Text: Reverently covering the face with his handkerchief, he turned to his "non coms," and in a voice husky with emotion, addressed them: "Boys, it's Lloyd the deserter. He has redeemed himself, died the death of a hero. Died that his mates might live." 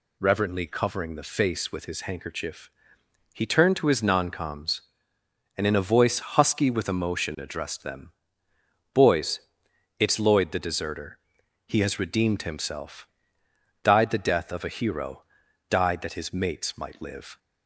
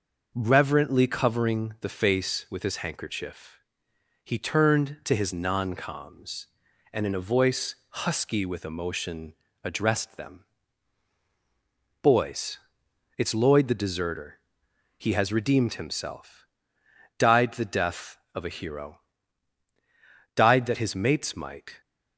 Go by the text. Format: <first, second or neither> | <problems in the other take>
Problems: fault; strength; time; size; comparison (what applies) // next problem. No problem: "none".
first | stops before "live"; at 21.8 s